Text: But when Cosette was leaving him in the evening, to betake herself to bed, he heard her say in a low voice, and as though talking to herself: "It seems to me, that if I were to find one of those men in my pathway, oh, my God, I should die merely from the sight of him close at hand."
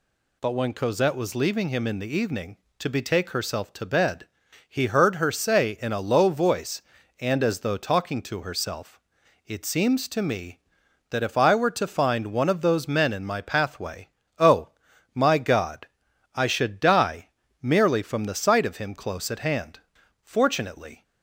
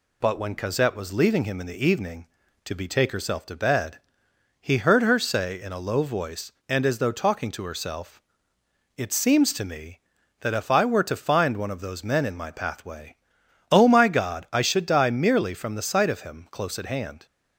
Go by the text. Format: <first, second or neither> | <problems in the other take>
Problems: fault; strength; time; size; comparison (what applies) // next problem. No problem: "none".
second | pauses between "die" and "merely"; slight; at 17.2 s; 0.32 s long // goes on to say "Fortunately"; noticeable; from 20.2 s on; 0.80 s long